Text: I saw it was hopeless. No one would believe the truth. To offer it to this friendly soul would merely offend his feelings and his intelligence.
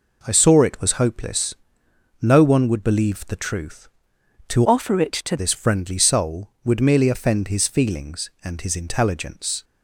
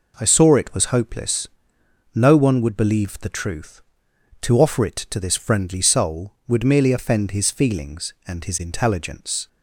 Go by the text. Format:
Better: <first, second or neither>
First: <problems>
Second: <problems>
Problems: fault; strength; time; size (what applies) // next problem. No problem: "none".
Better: second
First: changes voice from "offer" to "to"; from 4.6 to 5.3 s; 0.7 s long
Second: none